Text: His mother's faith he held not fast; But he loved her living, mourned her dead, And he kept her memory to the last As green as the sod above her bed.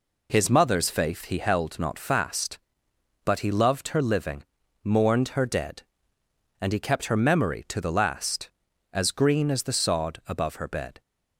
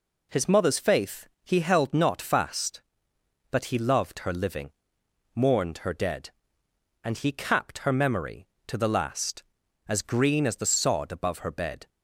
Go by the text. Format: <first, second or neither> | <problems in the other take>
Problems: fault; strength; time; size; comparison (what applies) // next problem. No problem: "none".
first | pauses between "faith" and "he"; slight; at 1.2 s; 0.16 s long // says "capped" for "kept"; at 7.3 s